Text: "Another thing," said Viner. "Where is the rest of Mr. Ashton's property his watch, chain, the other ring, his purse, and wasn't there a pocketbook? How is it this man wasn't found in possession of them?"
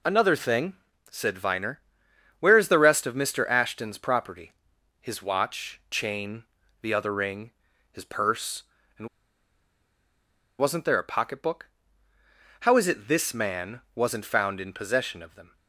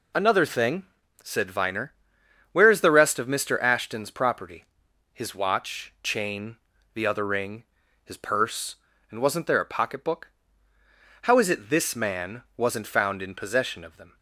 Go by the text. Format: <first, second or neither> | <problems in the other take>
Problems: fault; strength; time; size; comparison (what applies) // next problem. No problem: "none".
second | pauses between "property" and "his"; noticeable; at 4.5 s; 0.48 s long; noticeable in the second // pauses between "and" and "wasn't"; strong; at 9.0 s; 1.5 s long // pauses between "man" and "wasn't"; slight; at 13.7 s; 0.16 s long; slight in the second